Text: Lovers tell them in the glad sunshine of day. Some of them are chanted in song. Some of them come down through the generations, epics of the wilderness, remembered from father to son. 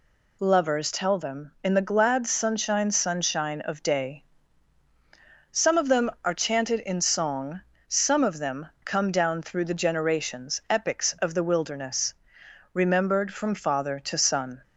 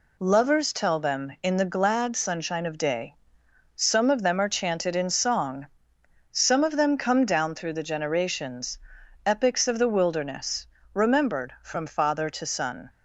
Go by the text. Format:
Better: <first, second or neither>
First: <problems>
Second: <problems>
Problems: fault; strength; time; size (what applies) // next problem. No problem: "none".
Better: second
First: says "sunshine" twice; at 2.9 s // pauses between "them" and "come"; slight; at 8.6 s; 0.16 s long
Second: none